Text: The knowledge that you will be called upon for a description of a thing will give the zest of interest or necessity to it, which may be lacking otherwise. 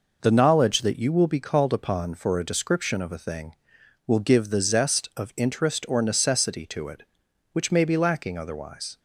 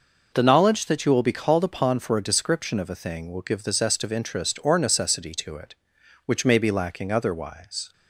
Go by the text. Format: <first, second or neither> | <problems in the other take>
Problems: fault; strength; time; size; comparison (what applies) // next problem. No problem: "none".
neither | none